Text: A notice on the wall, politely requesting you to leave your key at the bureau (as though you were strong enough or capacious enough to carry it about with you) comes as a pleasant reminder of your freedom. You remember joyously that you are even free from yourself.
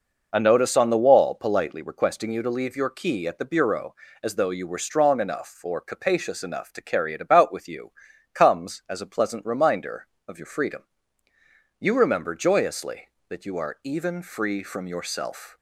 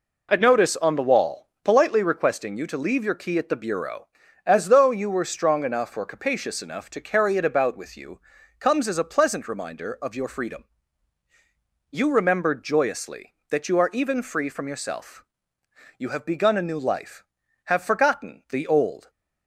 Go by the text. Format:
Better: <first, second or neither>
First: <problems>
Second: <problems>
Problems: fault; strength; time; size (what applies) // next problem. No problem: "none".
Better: first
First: none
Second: goes on to say "You have begun a new life have forgotten the old"; strong; from 15.9 s on; 3.1 s long